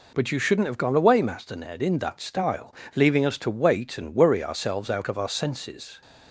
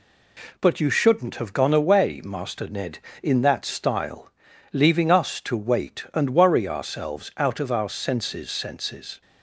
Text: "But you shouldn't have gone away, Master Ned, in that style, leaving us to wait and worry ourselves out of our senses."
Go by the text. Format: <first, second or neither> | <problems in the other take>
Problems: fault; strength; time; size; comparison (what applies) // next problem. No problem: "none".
first | says "senses" twice; at 8.5 s